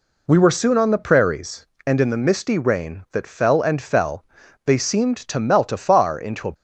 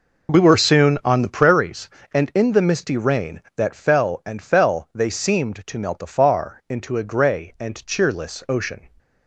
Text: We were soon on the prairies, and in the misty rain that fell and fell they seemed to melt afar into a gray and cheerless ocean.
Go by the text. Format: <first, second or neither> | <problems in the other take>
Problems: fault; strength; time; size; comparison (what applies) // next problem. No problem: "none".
second | pauses between "fell" and "they"; at 4.2 s; 0.40 s long // stops before "gray and cheerless ocean"; at 6.5 s